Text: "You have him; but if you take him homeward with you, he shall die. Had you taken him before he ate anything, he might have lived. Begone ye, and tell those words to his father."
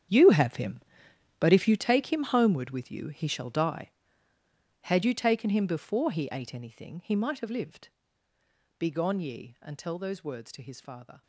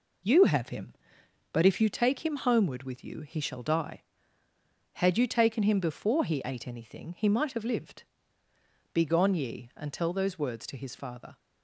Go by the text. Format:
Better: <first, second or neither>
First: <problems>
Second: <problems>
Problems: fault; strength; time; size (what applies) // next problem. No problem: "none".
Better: second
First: gets quieter; strong; throughout; 15 dB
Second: none